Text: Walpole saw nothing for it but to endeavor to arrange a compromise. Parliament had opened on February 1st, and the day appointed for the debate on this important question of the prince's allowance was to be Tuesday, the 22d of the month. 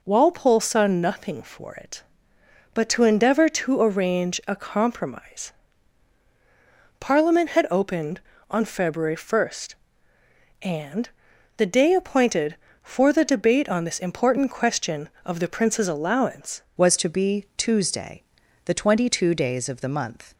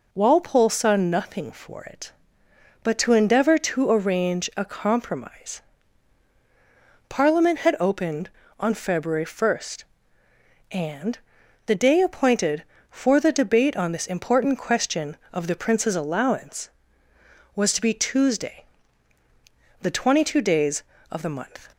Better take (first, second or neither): second